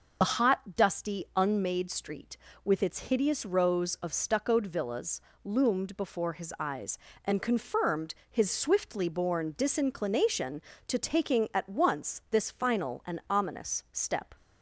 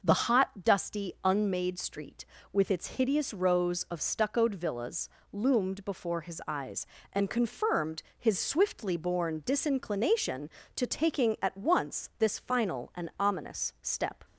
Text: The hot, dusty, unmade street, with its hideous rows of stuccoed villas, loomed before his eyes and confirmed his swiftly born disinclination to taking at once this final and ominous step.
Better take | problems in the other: second | loses the start of "The"; at 0.2 s; 70 ms // pauses between "confirmed" and "his"; slight; at 8.1 s; 0.16 s long; slight in the second

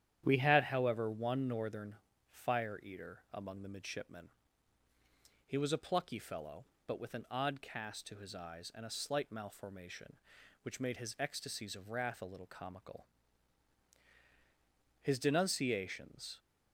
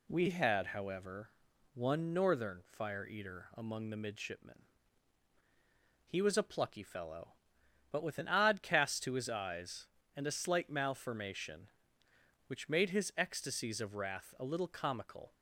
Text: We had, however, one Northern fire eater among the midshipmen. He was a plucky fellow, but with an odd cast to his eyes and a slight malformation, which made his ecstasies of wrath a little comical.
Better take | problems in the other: second | starts louder than the rest; strong; until 1.2 s; 10 dB // pauses between "Northern" and "fire"; slight; at 1.9 s; 0.34 s long // goes on to say "His denunciations"; from 15.0 s on; 1.3 s long

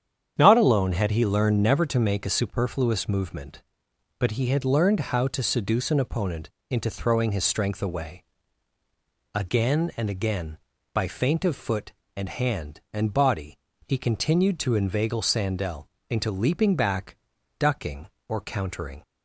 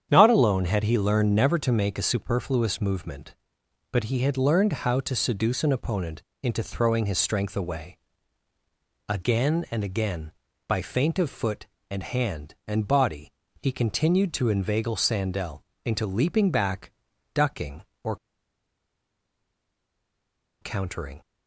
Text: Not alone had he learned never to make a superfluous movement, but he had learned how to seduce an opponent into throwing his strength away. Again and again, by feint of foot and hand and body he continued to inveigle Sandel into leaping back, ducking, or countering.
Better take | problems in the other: first | starts louder than the rest; strong; until 1.1 s; 8.5 dB; strong in the first // pauses between "opponent" and "into"; slight; at 6.2 s; 0.22 s long; slight in the first // pauses between "body" and "he"; slight; at 13.3 s; 0.30 s long; slight in the first // pauses between "Sandel" and "into"; slight; at 15.6 s; 0.20 s long; slight in the first // pauses between "or" and "countering"; strong; at 18.1 s; 2.4 s long

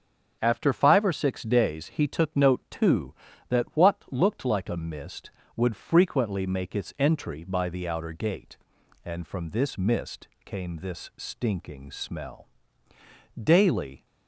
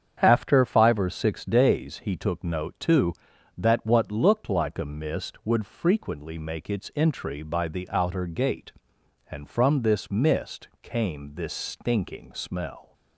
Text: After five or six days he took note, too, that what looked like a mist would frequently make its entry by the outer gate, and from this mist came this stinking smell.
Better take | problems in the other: second | starts louder than the rest; strong; until 1.4 s; 8 dB; strong in the second // pauses between "mist" and "came"; slight; at 10.2 s; 0.18 s long // goes on to say "Daily"; noticeable; from 13.4 s on; 0.64 s long

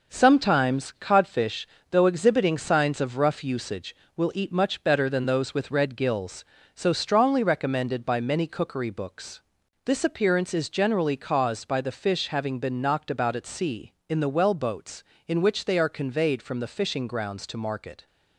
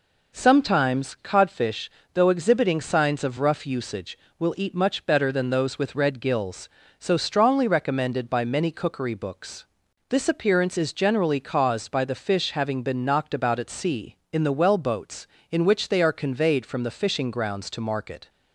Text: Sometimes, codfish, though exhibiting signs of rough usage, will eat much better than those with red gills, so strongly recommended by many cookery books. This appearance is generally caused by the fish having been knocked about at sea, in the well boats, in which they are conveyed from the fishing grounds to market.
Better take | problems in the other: second | gets quieter; throughout; 6.5 dB

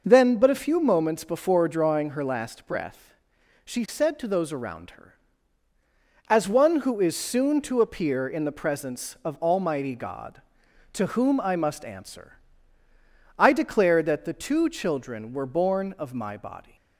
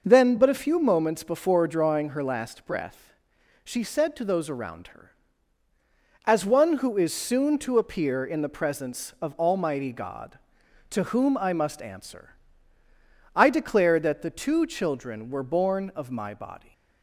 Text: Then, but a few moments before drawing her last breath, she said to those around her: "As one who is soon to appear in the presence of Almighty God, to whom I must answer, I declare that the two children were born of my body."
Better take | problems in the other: neither | none

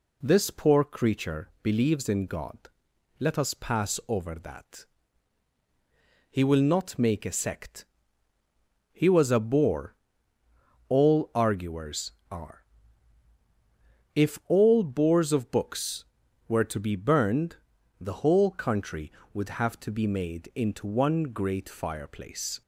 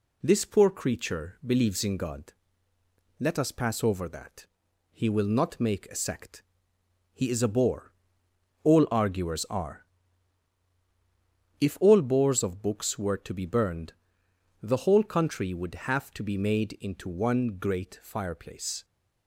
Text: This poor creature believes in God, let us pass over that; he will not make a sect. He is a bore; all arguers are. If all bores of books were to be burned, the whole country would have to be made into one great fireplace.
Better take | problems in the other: second | says "was" for "is"; at 9.0 s

